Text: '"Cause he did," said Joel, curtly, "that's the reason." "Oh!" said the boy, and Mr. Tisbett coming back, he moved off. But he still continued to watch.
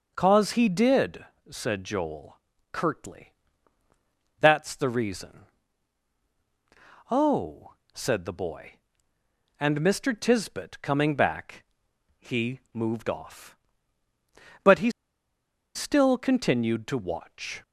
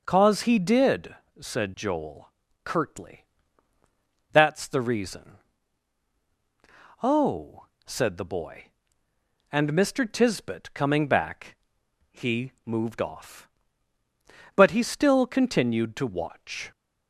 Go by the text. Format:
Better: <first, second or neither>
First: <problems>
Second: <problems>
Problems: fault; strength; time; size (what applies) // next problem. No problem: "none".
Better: second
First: pauses between "he" and "moved"; slight; at 12.5 s; 0.16 s long // pauses between "he" and "still"; noticeable; at 14.9 s; 0.84 s long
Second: pauses between "he" and "moved"; slight; at 12.5 s; 0.16 s long